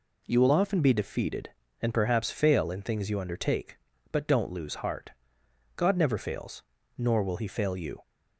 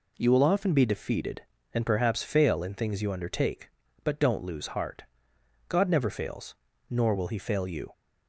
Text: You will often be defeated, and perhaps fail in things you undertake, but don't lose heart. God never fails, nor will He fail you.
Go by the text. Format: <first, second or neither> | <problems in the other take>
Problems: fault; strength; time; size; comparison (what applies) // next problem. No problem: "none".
neither | none